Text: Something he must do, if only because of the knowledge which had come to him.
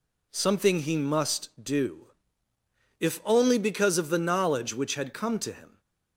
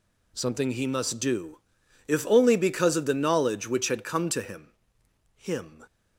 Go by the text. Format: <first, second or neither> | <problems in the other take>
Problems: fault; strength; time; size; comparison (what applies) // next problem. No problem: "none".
first | says "him" twice; at 5.3 s